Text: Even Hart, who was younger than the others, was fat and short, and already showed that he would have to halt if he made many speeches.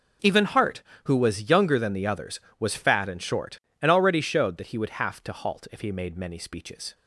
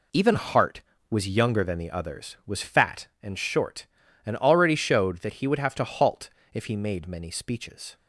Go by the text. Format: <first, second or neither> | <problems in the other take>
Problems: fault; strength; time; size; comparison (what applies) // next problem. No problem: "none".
first | skips "who"; at 0.9 s // pauses between "halt" and "if"; slight; at 6.2 s; 0.22 s long